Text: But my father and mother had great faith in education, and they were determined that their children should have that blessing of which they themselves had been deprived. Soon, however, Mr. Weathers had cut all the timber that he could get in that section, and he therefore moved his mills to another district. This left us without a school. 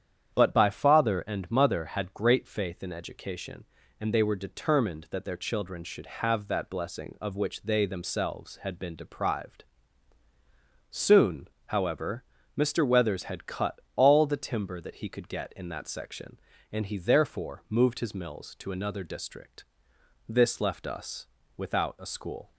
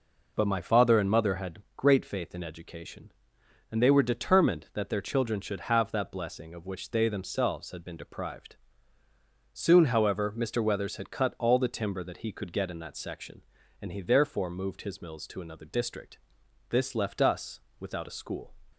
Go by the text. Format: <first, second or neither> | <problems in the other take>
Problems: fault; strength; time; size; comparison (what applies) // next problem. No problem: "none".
second | starts louder than the rest; strong; until 1.3 s; 9 dB // says "by" for "my"; at 0.5 s // pauses between "cut" and "all"; slight; at 13.7 s; 0.18 s long // pauses between "us" and "without"; slight; at 21.2 s; 0.30 s long; slight in the second